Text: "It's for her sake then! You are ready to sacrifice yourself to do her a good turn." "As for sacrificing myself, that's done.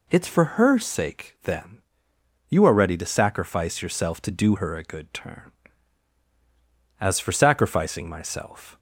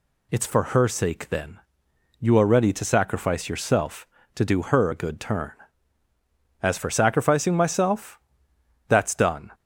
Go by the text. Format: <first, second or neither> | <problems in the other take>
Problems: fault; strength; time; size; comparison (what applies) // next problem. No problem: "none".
second | stops before "that's done"; at 8.7 s